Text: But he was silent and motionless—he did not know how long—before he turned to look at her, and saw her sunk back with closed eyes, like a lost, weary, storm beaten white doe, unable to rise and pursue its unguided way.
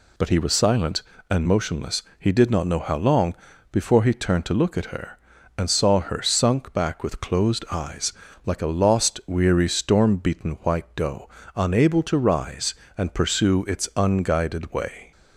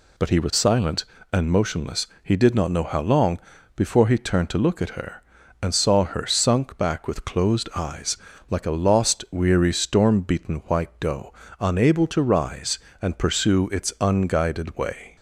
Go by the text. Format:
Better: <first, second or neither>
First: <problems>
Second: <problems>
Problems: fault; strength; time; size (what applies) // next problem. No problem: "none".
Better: neither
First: none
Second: none